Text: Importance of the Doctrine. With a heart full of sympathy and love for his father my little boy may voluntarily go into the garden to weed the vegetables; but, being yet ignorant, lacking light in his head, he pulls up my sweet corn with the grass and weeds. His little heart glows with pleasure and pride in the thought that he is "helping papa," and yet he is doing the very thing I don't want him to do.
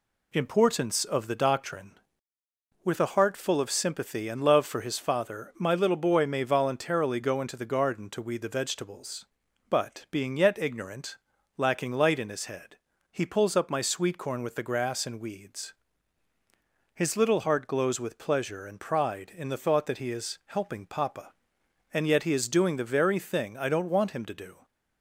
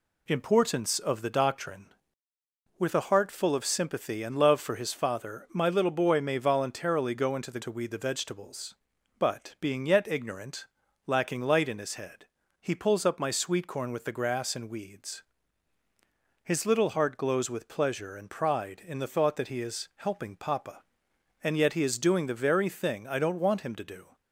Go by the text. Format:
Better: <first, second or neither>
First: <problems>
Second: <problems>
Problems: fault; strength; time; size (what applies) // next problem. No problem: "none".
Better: first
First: none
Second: skips "garden"; at 7.6 s